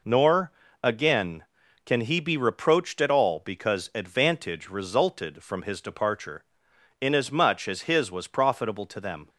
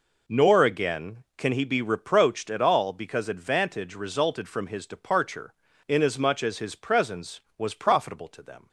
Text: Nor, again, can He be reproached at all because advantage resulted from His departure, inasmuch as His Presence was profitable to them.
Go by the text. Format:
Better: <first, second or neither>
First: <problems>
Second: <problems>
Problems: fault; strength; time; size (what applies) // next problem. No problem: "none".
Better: second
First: skips "Presence"; at 8.1 s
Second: none